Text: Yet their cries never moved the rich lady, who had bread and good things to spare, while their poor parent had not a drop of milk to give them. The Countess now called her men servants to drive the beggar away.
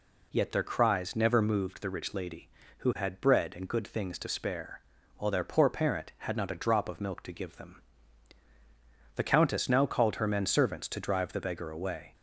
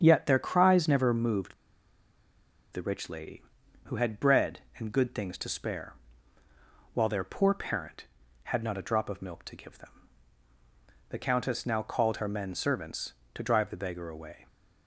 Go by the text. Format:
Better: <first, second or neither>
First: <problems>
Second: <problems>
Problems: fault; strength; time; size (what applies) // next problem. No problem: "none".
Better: first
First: none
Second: starts louder than the rest; strong; until 1.0 s; 7.5 dB // pauses between "moved" and "the"; at 1.5 s; 1.1 s long